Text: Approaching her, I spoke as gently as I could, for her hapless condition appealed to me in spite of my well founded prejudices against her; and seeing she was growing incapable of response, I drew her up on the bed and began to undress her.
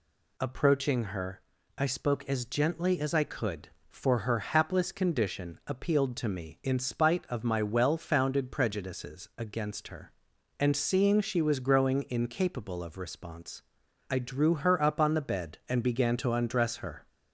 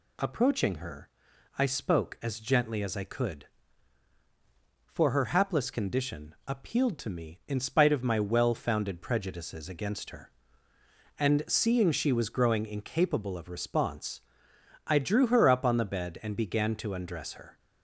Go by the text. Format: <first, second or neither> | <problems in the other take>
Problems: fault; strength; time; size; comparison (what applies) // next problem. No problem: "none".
neither | none